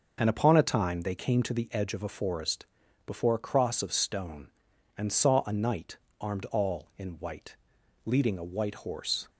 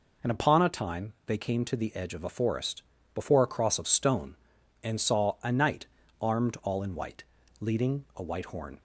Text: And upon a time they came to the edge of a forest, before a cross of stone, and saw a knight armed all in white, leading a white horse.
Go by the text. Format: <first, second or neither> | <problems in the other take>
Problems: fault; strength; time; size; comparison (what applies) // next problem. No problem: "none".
first | pauses between "knight" and "armed"; slight; at 5.8 s; 0.34 s long; slight in the first // says "horn" for "horse"; at 8.4 s